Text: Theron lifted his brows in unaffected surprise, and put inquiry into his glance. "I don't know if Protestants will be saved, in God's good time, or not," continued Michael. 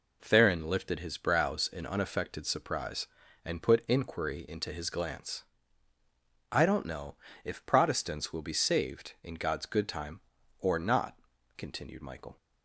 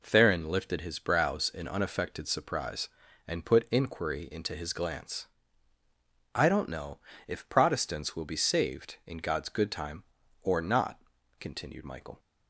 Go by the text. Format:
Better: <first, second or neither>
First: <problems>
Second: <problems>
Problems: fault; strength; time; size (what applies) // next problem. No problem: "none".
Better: neither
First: pauses between "know" and "if"; slight; at 7.1 s; 0.30 s long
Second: pauses between "know" and "if"; slight; at 6.9 s; 0.30 s long